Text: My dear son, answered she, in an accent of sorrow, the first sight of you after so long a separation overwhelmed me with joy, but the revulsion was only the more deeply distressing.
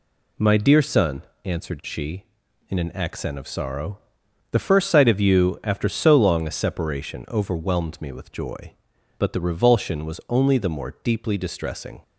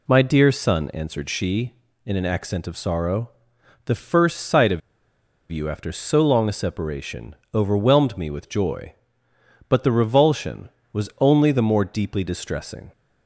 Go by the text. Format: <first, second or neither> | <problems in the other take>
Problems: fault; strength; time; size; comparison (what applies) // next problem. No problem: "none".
first | pauses between "of" and "you"; noticeable; at 4.8 s; 0.69 s long // pauses between "separation" and "overwhelmed"; slight; at 7.3 s; 0.20 s long